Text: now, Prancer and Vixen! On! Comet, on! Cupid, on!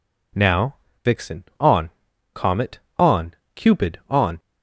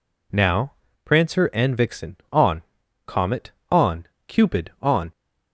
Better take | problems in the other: second | skips "Prancer and"; at 0.8 s

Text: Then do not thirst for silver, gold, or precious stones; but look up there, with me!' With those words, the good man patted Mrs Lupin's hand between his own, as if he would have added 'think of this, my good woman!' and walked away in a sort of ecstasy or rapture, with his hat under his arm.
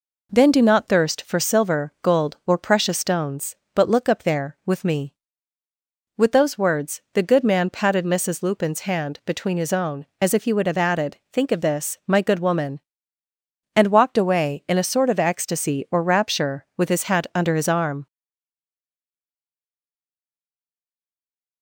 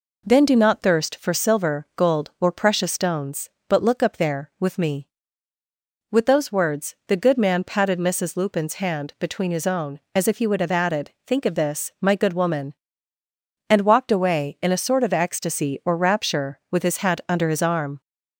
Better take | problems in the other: second | pauses between "added" and "think"; slight; at 11.1 s; 0.16 s long; slight in the second // stays silent after the last word; strong; from 18.0 s on; 3.6 s long

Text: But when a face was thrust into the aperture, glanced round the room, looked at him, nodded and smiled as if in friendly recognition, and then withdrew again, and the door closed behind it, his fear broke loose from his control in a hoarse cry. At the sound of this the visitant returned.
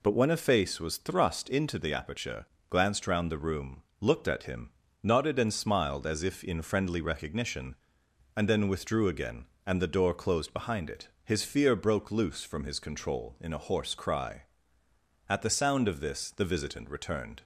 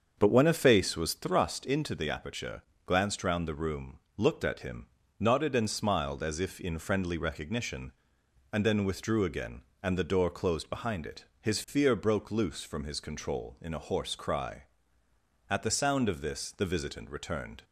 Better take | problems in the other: first | starts louder than the rest; until 1.3 s; 7 dB

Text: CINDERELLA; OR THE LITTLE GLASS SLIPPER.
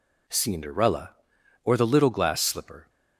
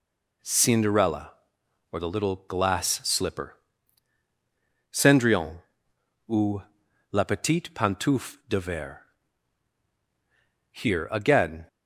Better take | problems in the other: first | goes on to say "Cendrillon ou la Petite Pantoufle de Verre Here again"; strong; from 4.9 s on; 6.7 s long

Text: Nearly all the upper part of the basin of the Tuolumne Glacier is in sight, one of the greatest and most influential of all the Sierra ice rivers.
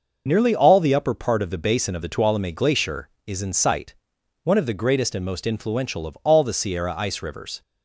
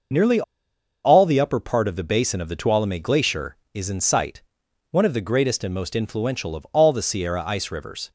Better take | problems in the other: first | pauses between "Nearly" and "all"; noticeable; at 0.4 s; 0.62 s long

